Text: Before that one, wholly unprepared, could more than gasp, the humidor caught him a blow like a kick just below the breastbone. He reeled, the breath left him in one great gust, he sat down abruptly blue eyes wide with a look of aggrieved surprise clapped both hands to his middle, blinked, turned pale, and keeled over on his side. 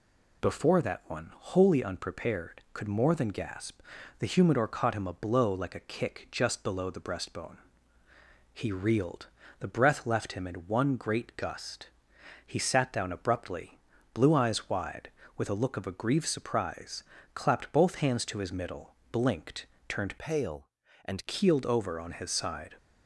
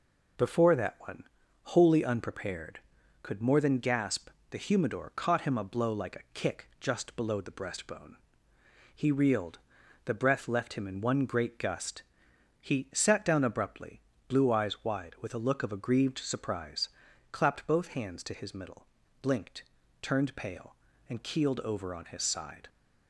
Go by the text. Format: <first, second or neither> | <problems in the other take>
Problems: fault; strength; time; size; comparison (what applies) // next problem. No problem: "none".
second | pauses between "abruptly" and "blue"; slight; at 13.7 s; 0.34 s long; slight in the second // pauses between "surprise" and "clapped"; slight; at 17.0 s; 0.32 s long; also in the second // changes voice from "pale" to "and"; from 20.1 to 21.2 s; 1.1 s long